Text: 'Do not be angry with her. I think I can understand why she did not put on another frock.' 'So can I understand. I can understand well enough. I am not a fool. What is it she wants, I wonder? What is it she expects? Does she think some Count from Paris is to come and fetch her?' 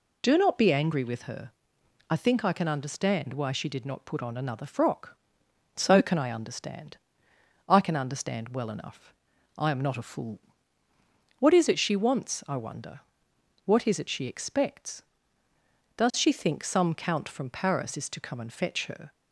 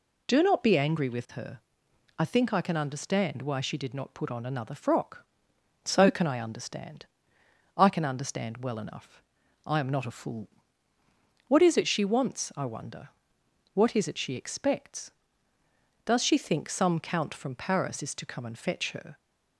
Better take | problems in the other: neither | none

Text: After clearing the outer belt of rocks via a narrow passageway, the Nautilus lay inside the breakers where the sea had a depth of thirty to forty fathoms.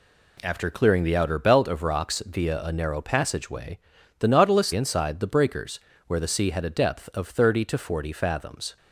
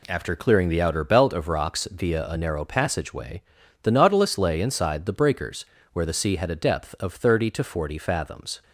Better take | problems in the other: second | skips "lay"; at 4.7 s // pauses between "breakers" and "where"; slight; at 5.7 s; 0.28 s long; slight in the second

